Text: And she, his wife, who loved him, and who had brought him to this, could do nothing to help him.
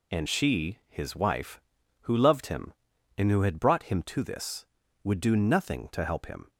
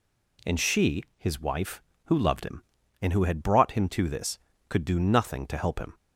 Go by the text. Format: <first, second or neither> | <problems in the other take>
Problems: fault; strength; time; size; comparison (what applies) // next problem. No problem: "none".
second | says "would" for "could"; at 5.0 s